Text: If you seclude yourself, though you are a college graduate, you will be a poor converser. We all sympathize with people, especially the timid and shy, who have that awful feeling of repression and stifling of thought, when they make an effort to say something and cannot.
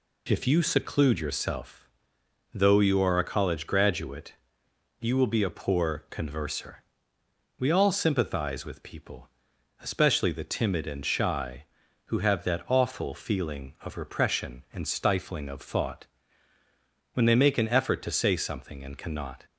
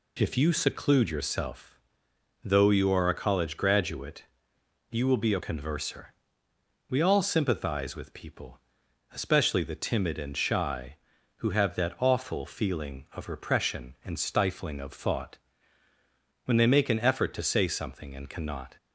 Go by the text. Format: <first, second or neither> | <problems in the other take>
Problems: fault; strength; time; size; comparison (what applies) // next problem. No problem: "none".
first | skips "poor"; at 5.3 s